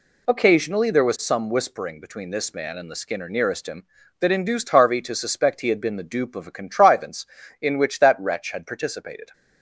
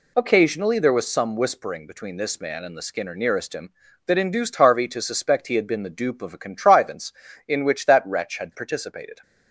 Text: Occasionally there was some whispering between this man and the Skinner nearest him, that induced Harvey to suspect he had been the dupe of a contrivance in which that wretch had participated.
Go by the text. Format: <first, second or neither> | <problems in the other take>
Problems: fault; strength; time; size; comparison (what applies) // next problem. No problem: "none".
neither | none